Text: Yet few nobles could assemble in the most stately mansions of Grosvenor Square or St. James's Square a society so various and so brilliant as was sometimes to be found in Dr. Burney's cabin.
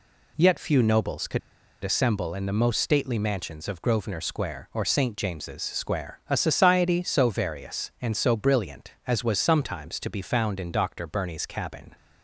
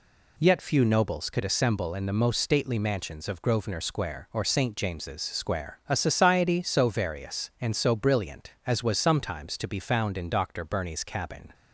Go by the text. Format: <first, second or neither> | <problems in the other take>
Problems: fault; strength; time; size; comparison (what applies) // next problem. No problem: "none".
second | pauses between "could" and "assemble"; at 1.3 s; 0.43 s long